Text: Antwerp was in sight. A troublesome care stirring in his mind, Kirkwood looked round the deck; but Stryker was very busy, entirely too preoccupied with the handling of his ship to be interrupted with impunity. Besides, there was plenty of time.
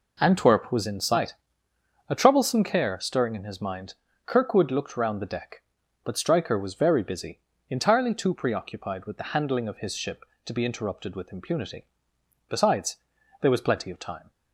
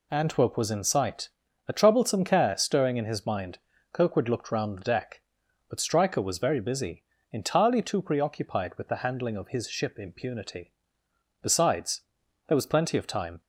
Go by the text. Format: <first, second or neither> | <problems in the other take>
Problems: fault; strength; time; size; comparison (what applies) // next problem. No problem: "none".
first | skips "to be interrupted with"; at 9.9 s